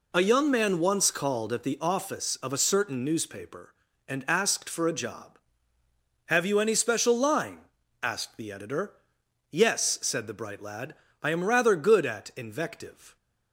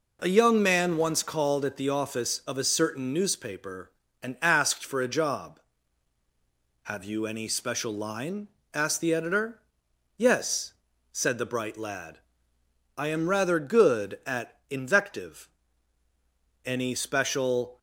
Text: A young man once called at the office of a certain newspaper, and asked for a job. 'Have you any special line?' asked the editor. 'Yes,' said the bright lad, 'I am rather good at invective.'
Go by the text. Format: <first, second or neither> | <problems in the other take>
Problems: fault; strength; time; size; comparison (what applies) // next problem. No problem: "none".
first | goes on to say "Any special"; noticeable; from 16.6 s on; 1.1 s long